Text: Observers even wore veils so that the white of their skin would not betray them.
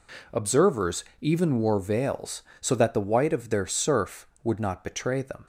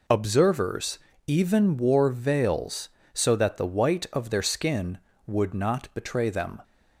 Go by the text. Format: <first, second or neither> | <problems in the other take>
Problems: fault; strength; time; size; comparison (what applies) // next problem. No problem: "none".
second | pauses between "Observers" and "even"; slight; at 1.0 s; 0.18 s long; slight in the second // says "surf" for "skin"; at 3.6 s